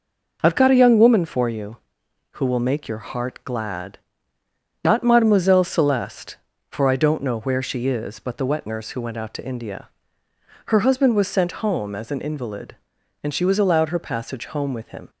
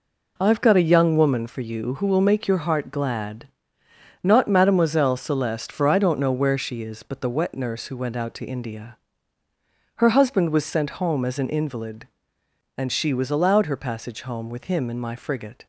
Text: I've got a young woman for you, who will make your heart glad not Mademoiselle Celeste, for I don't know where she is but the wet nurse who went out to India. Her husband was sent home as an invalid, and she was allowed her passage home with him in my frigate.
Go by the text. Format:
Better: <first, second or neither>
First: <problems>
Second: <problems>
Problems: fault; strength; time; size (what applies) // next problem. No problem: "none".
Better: second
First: pauses between "glad" and "not"; noticeable; at 3.9 s; 0.84 s long // stops before "in my frigate"; at 15.0 s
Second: pauses between "glad" and "not"; noticeable; at 3.4 s; 0.74 s long